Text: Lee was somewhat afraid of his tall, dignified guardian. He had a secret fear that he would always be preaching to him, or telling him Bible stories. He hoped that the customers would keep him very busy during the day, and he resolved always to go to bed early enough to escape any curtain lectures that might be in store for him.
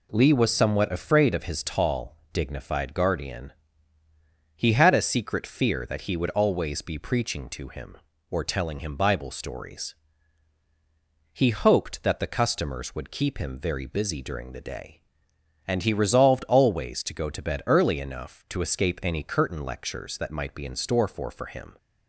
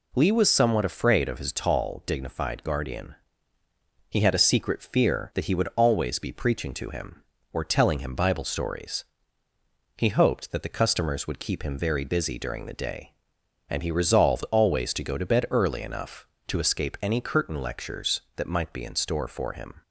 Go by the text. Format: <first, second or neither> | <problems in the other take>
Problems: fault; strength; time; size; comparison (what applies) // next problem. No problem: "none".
second | says "for" twice; at 21.3 s